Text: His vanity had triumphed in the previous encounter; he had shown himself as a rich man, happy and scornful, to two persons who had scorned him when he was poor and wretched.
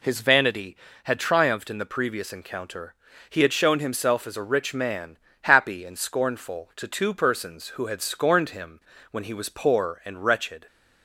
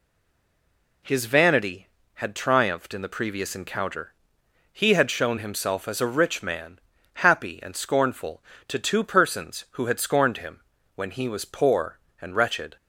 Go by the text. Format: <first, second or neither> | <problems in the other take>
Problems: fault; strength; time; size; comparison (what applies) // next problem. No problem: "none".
first | stays silent before the first word; until 1.0 s; 1.0 s long // pauses between "him" and "when"; slight; at 10.6 s; 0.34 s long; slight in the first